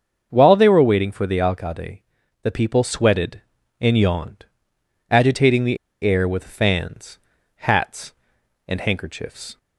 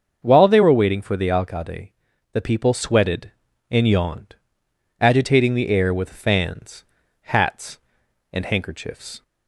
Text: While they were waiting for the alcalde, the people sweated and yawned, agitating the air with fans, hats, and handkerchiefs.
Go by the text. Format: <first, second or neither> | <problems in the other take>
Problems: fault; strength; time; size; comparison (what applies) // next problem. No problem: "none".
second | starts louder than the rest; until 1.3 s; 7 dB; also in the second // pauses between "the" and "air"; slight; at 5.7 s; 0.26 s long